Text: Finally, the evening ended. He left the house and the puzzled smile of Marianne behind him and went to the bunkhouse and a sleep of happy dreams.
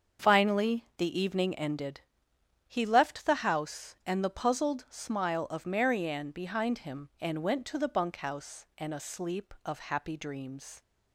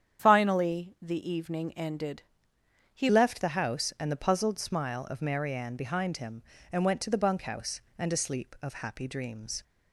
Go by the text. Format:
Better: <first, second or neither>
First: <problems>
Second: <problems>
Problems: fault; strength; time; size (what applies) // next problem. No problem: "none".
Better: first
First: starts louder than the rest; until 1.3 s; 7 dB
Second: starts louder than the rest; strong; until 1.2 s; 8.5 dB // changes voice at "left"; from 3.0 s on; 6.6 s long